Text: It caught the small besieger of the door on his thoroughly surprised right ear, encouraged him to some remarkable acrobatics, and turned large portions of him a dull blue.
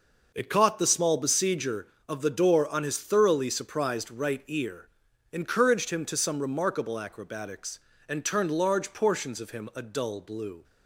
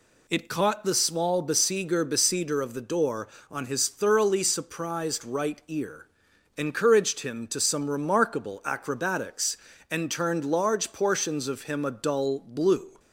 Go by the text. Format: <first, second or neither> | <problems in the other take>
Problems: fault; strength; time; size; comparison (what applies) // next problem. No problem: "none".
first | says "besieger" twice; at 2.0 s